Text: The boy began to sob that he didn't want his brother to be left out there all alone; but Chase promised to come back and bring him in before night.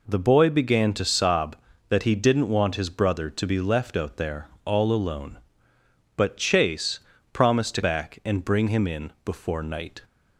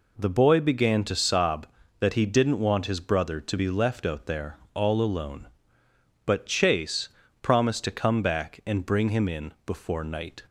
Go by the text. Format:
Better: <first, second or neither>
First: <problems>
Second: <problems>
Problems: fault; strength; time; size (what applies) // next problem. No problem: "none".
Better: second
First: pauses between "there" and "all"; slight; at 4.4 s; 0.18 s long // pauses between "Chase" and "promised"; slight; at 7.0 s; 0.32 s long // skips "come"; at 7.8 s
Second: pauses between "there" and "all"; slight; at 4.5 s; 0.18 s long // pauses between "Chase" and "promised"; slight; at 7.0 s; 0.32 s long